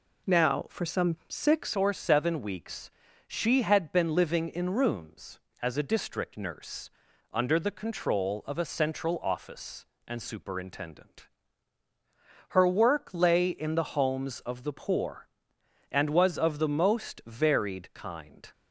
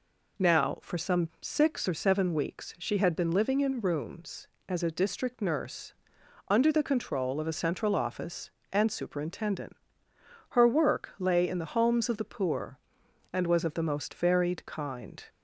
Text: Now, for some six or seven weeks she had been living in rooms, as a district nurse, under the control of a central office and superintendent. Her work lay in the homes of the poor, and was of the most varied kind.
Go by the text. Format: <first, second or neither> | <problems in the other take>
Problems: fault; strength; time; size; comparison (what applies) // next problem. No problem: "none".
second | changes voice at "or"; from 1.7 s on; 16.8 s long // pauses between "weeks" and "she"; at 2.9 s; 0.38 s long